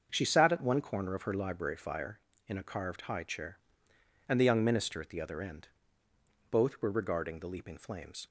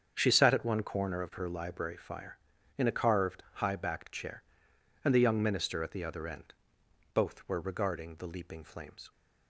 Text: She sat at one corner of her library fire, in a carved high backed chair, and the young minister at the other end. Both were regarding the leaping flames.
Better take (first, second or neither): second